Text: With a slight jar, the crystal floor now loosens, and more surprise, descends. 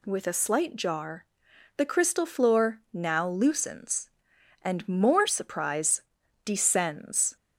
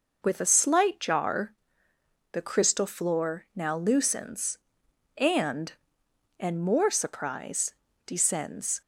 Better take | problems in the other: first | says "and" twice; at 6.3 s

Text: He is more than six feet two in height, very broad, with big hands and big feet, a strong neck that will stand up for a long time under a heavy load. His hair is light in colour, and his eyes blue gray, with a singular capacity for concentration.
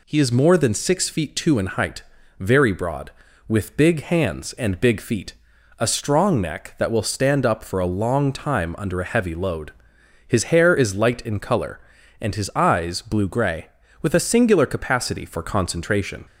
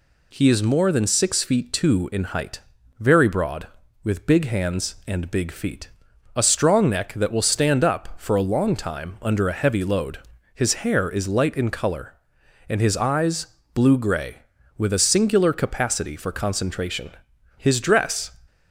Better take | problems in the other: first | pauses between "eyes" and "blue"; slight; at 13.4 s; 0.26 s long // goes on to say "His dress"; noticeable; from 17.5 s on; 0.74 s long

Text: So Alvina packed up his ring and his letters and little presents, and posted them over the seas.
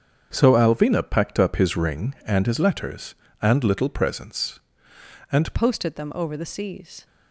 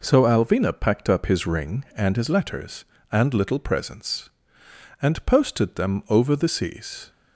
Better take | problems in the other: second | starts louder than the rest; strong; until 1.3 s; 7.5 dB // changes voice at "posted"; from 5.5 s on; 1.5 s long

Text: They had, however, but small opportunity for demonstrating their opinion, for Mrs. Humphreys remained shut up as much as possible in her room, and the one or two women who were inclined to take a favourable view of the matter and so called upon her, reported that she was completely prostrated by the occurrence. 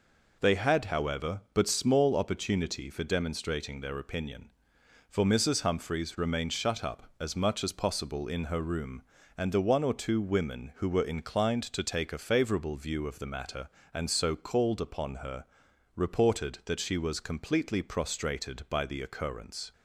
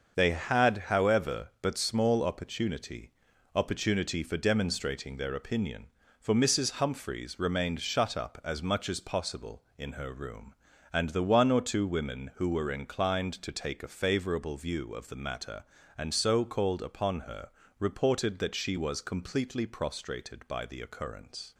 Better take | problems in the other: first | starts louder than the rest; until 1.2 s; 6.5 dB // says "opportunity" twice; at 3.5 s

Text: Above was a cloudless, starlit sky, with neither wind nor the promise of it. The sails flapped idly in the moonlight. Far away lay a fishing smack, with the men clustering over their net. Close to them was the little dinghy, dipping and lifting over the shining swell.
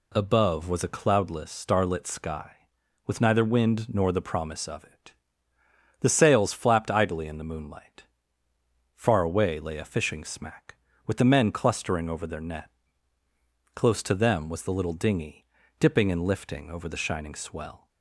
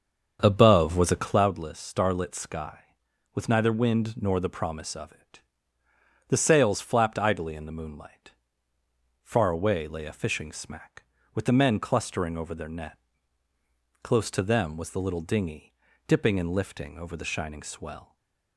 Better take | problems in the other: first | starts louder than the rest; until 1.6 s; 7 dB // stays silent after the last word; slight; from 18.0 s on; 0.5 s long

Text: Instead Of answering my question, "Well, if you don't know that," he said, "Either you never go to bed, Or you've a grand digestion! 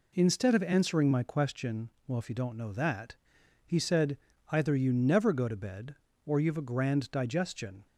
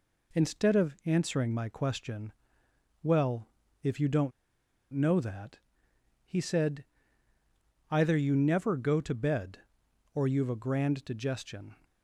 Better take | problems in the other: first | pauses between "don't" and "know"; noticeable; at 4.3 s; 0.60 s long

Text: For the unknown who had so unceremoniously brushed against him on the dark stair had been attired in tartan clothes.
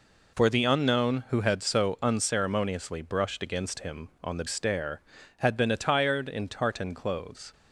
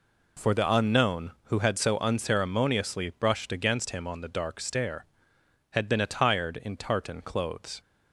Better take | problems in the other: second | skips "dark"; at 4.4 s

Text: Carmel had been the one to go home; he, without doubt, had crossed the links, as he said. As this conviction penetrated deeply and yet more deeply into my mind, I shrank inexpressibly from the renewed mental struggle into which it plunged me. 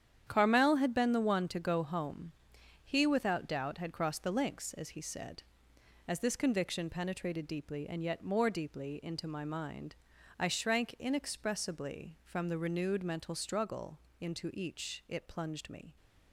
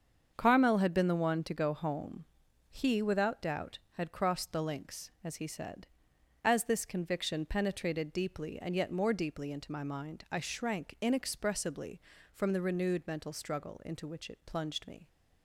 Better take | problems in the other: second | starts louder than the rest; strong; until 1.2 s; 9 dB; also in the second // pauses between "struggle" and "into"; slight; at 13.9 s; 0.20 s long // says "each" for "which"; at 14.5 s

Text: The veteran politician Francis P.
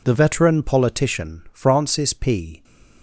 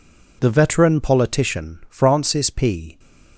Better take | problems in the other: neither | none

